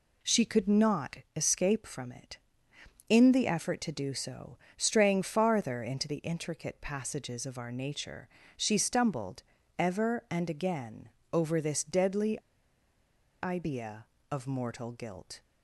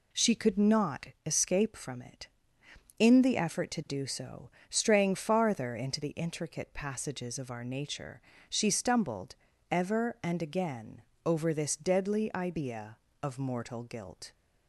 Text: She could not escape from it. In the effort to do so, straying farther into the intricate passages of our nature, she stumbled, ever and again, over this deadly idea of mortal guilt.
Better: second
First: pauses between "not" and "escape"; slight; at 1.1 s; 0.18 s long // pauses between "deadly" and "idea"; at 12.4 s; 1.0 s long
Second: pauses between "not" and "escape"; slight; at 1.0 s; 0.18 s long

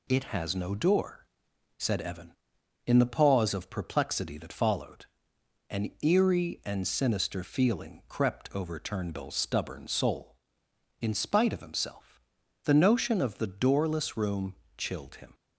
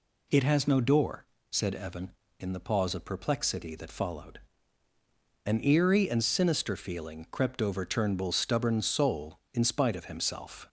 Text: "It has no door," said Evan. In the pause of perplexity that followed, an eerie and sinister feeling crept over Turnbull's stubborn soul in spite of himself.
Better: second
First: goes on to say "The notion of the doorless room chilled him"; strong; from 12.6 s on; 2.7 s long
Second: none

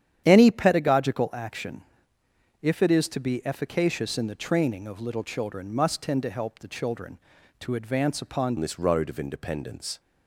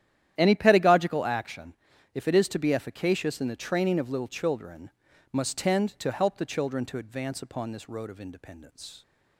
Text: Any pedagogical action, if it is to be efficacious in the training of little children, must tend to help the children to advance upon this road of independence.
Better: second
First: starts louder than the rest; strong; until 1.2 s; 9.5 dB // changes voice at "this"; from 8.5 s on; 1.4 s long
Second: starts louder than the rest; strong; until 1.3 s; 11 dB

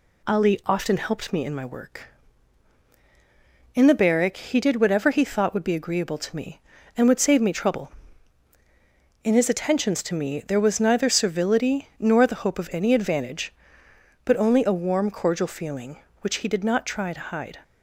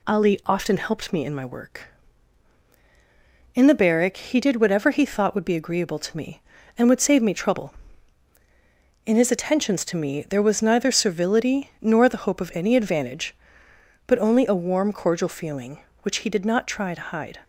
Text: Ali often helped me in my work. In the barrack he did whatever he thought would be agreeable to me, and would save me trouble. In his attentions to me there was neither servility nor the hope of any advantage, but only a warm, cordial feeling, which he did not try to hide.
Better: neither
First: none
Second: none

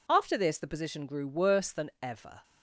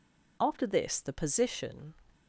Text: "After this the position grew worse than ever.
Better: first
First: none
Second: stops before "grew worse than ever"; at 2.1 s

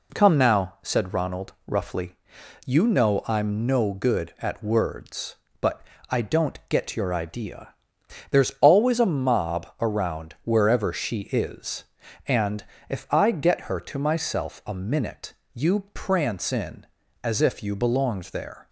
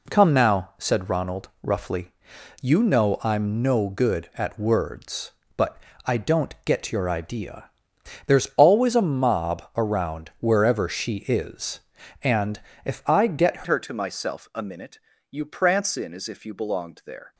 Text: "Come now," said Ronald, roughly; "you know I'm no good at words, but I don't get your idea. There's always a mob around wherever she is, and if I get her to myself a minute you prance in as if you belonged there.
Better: first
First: pauses between "but" and "I"; slight; at 5.8 s; 0.26 s long // pauses between "and" and "if"; slight; at 12.6 s; 0.24 s long // pauses between "minute" and "you"; slight; at 15.3 s; 0.20 s long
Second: pauses between "but" and "I"; slight; at 5.7 s; 0.26 s long // pauses between "and" and "if"; slight; at 12.6 s; 0.24 s long // changes voice at "her"; from 13.6 s on; 3.7 s long // pauses between "minute" and "you"; slight; at 14.9 s; 0.32 s long

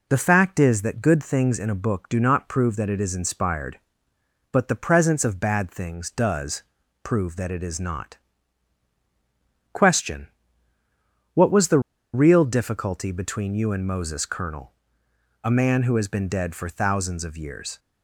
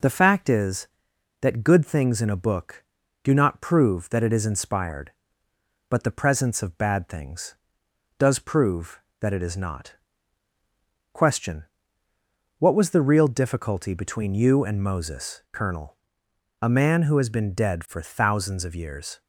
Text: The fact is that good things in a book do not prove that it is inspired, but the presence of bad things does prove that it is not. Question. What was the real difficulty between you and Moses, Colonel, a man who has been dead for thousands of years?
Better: second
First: pauses between "does" and "prove"; at 6.6 s; 0.40 s long // pauses between "the" and "real"; slight; at 11.7 s; 0.34 s long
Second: none

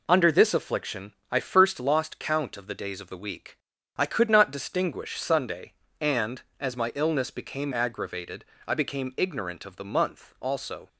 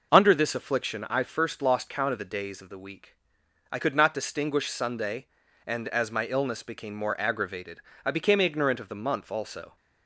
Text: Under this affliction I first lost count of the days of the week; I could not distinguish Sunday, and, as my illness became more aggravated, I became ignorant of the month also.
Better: second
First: pauses between "affliction" and "I"; slight; at 1.1 s; 0.18 s long // skips "more"; at 7.7 s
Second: none

